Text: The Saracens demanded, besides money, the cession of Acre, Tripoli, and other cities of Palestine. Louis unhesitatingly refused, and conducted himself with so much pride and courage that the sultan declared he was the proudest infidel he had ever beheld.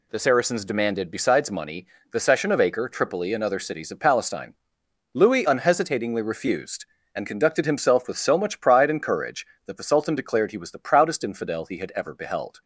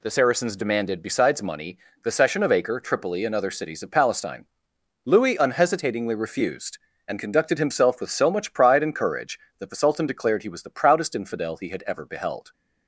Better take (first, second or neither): neither